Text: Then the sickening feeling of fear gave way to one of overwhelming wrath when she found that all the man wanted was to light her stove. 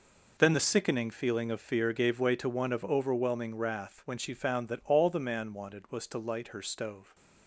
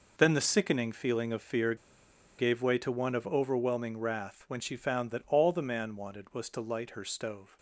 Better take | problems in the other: first | pauses between "fear" and "gave"; noticeable; at 1.7 s; 0.63 s long

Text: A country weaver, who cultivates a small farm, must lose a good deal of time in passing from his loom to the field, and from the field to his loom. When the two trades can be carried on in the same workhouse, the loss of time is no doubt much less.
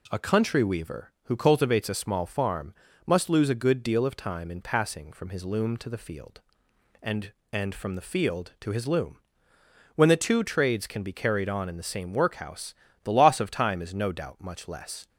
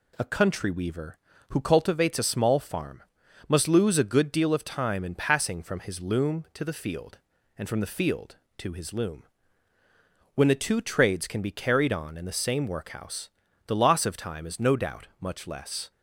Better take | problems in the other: second | says "and" twice; at 7.5 s

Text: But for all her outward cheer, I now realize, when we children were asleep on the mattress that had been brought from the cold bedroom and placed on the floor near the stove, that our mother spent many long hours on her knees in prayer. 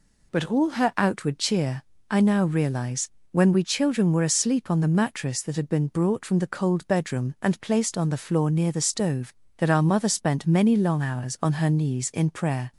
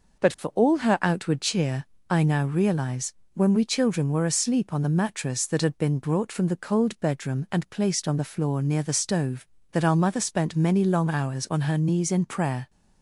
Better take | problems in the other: second | skips "for"; at 0.5 s

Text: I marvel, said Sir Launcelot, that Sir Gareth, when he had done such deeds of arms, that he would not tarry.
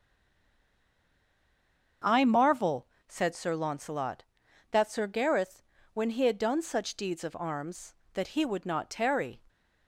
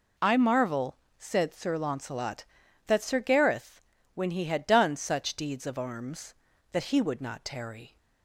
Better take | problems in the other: second | stays silent before the first word; noticeable; until 2.0 s; 2.0 s long // starts louder than the rest; until 3.2 s; 7 dB

